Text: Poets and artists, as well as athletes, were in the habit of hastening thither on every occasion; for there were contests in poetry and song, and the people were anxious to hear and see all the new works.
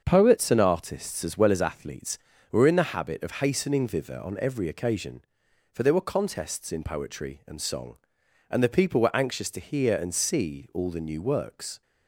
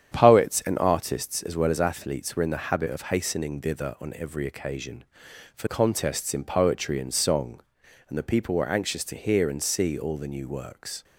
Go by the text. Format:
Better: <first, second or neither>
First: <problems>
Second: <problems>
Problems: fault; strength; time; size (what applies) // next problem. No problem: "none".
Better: first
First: starts louder than the rest; until 1.0 s; 7 dB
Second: starts louder than the rest; strong; until 1.1 s; 9 dB // skips "there were"; at 5.6 s